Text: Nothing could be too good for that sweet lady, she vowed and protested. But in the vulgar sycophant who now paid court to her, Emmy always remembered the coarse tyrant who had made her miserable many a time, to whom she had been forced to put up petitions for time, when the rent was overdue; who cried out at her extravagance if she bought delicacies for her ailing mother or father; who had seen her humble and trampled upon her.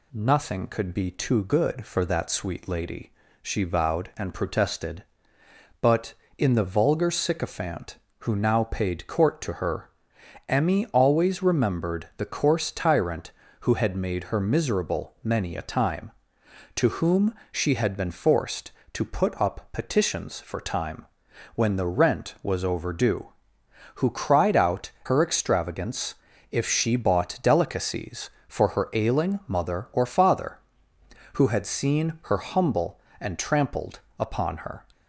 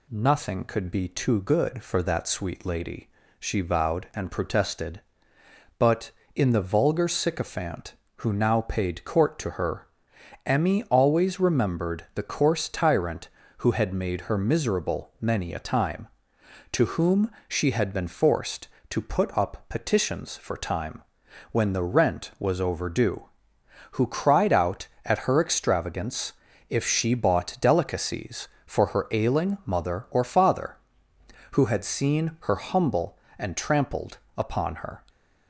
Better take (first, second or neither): second